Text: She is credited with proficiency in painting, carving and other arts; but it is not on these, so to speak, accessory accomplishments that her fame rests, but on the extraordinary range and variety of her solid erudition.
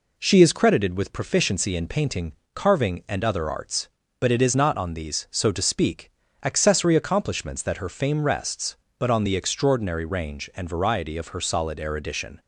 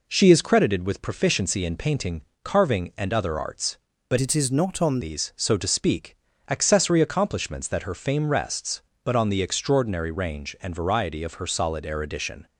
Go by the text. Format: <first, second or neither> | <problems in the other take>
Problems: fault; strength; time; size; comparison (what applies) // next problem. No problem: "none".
first | changes voice from "it" to "on"; from 4.1 to 4.9 s; 0.8 s long